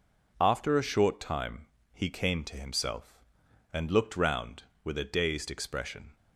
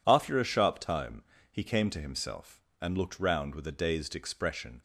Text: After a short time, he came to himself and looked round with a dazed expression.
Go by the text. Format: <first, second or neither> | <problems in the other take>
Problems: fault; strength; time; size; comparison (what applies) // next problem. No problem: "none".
first | says "sharp" for "short"; at 0.4 s